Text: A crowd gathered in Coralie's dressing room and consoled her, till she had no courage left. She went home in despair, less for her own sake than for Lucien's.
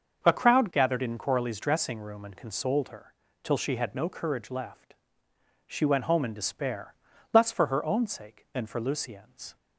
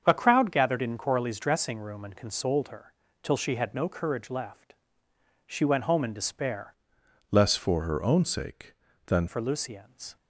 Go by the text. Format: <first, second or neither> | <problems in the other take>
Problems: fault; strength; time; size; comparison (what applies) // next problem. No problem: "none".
first | starts louder than the rest; strong; until 1.0 s; 7.5 dB; also in the first // changes voice from "less" to "than"; from 7.3 to 9.2 s; 1.9 s long